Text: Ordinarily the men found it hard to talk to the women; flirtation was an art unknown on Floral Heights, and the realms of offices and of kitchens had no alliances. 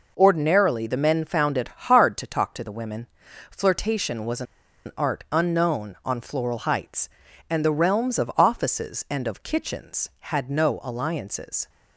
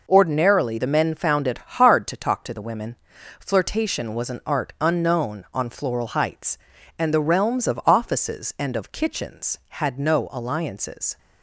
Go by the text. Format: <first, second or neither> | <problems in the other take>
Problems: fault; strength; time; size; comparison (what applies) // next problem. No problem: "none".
second | pauses between "it" and "hard"; slight; at 1.6 s; 0.20 s long; slight in the second // pauses between "was" and "an"; at 4.4 s; 0.43 s long